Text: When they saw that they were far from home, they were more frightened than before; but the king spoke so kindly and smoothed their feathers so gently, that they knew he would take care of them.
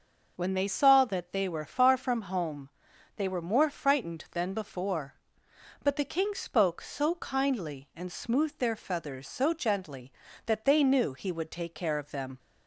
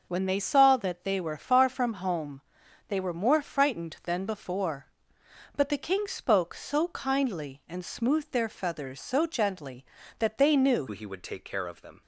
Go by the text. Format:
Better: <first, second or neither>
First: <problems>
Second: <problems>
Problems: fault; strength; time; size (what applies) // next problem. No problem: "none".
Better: first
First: none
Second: changes voice at "he"; from 10.8 s on; 1.2 s long